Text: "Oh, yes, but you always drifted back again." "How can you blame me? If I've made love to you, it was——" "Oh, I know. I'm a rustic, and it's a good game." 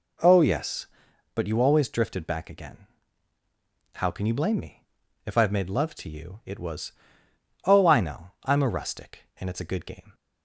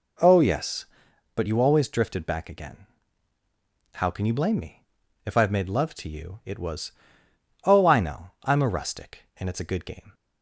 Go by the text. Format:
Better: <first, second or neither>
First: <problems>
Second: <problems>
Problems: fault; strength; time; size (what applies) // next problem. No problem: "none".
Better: neither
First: none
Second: none